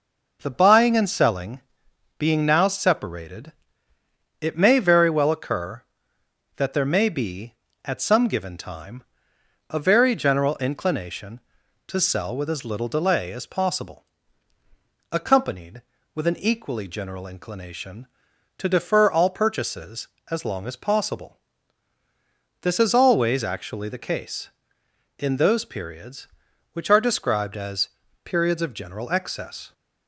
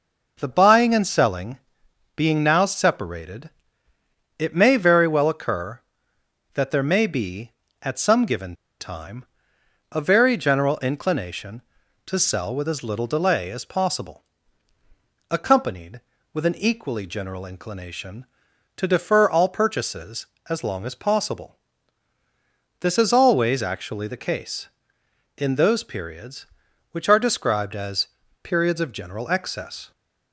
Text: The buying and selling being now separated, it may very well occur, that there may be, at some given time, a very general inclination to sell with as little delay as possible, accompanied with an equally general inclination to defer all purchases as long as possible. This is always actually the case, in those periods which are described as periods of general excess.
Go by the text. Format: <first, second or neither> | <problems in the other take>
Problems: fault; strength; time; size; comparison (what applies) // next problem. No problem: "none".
first | pauses between "selling" and "being"; noticeable; at 1.5 s; 0.58 s long; noticeable in the first // pauses between "given" and "time"; slight; at 8.5 s; 0.26 s long // pauses between "as" and "periods"; slight; at 28.0 s; 0.36 s long; slight in the first